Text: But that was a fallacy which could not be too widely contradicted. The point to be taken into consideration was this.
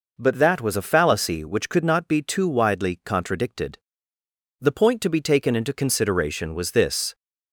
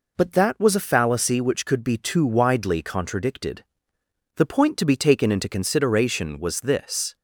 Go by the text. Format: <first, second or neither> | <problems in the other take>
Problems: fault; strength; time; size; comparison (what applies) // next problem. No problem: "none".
first | skips "not"; at 1.8 s